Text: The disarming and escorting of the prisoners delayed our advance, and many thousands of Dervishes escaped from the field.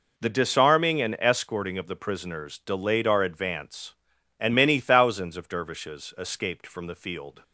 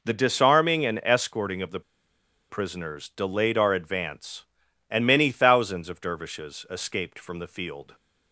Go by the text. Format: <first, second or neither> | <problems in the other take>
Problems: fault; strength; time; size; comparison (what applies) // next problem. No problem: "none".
first | pauses between "the" and "prisoners"; noticeable; at 1.8 s; 0.69 s long